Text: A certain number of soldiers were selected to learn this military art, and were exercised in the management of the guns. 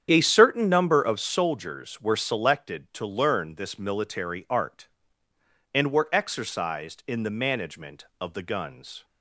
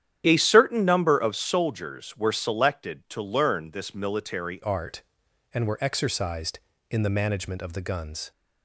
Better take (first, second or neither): first